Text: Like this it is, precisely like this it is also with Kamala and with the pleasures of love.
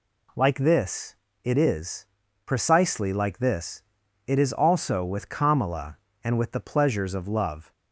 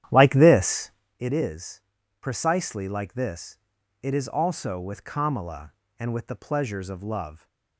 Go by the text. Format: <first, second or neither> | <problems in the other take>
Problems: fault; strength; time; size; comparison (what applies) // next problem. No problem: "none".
first | starts louder than the rest; strong; until 1.2 s; 11 dB // pauses between "this" and "it"; slight; at 0.9 s; 0.28 s long; slight in the first // pauses between "this" and "it"; noticeable; at 3.5 s; 0.46 s long; noticeable in the first